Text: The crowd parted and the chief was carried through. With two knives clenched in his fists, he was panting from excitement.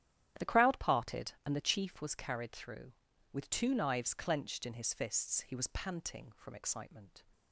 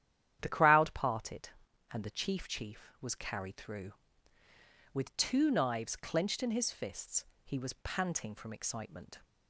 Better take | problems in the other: first | starts louder than the rest; strong; until 1.4 s; 10.5 dB; strong in the first // says "chief" twice; at 2.4 s

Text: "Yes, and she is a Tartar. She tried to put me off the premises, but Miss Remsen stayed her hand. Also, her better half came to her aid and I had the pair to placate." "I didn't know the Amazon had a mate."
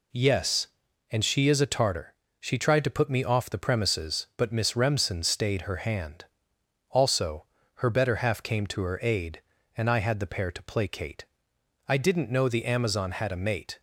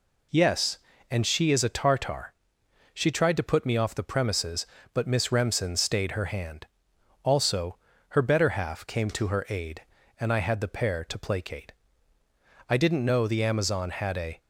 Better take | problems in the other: first | stops before "mate"; at 14.3 s

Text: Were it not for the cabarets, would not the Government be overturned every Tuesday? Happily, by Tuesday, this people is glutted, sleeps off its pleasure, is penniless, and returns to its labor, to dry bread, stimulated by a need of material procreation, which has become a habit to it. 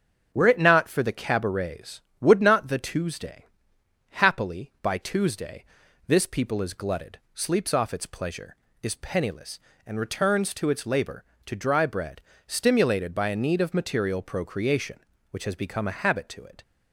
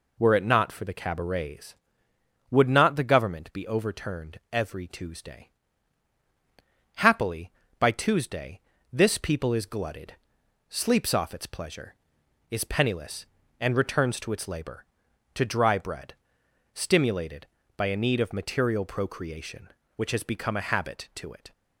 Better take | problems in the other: second | starts louder than the rest; strong; until 1.3 s; 7.5 dB // skips "Government be overturned every"; at 2.7 s

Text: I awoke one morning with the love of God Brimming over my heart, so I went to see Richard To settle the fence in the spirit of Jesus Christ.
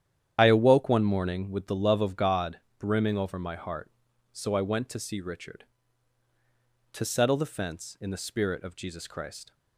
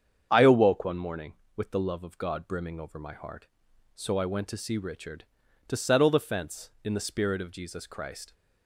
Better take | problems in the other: second | loses the start of "I"; at 0.3 s; 30 ms // starts louder than the rest; strong; until 1.3 s; 10 dB; strong in the second // pauses between "God" and "Brimming"; slight; at 2.5 s; 0.20 s long

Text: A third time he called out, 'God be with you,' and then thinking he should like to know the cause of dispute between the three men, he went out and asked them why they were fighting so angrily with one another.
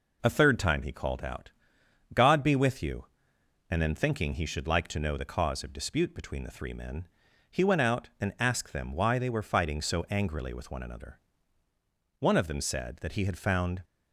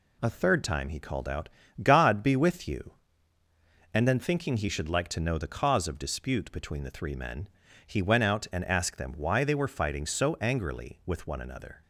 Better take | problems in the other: second | goes on to say "One of them said that he had found"; from 12.1 s on; 1.6 s long

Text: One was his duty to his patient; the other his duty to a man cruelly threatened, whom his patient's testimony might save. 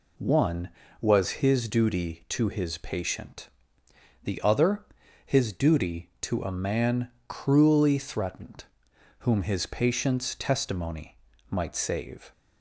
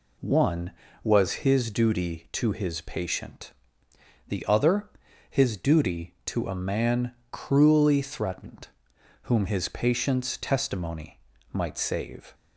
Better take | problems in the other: neither | pauses between "other" and "his"; the same in both // pauses between "man" and "cruelly"; slight; the same in both // pauses between "testimony" and "might"; slight; the same in both

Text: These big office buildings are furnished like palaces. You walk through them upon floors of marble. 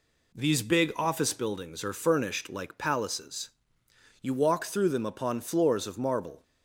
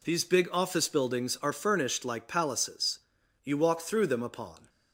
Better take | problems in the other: first | stops before "floors of marble"; at 4.6 s

